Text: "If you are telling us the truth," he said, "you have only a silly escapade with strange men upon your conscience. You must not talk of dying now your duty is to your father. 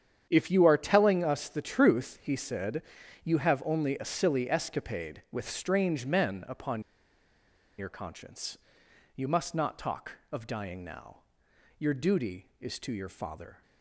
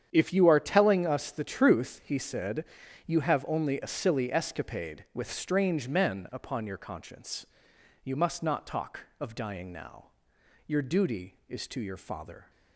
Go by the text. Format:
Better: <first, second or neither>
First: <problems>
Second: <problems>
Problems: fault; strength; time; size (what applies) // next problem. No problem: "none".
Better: second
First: starts louder than the rest; strong; until 1.3 s; 8.5 dB // pauses between "upon" and "your"; noticeable; at 6.8 s; 0.96 s long // pauses between "now" and "your"; noticeable; at 11.1 s; 0.60 s long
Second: starts louder than the rest; strong; until 1.1 s; 8.5 dB // pauses between "now" and "your"; noticeable; at 10.0 s; 0.60 s long